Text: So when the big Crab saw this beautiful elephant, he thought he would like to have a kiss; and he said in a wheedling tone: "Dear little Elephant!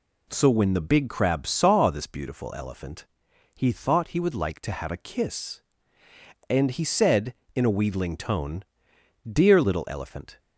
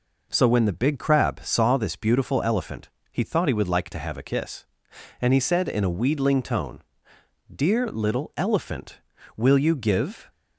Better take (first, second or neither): first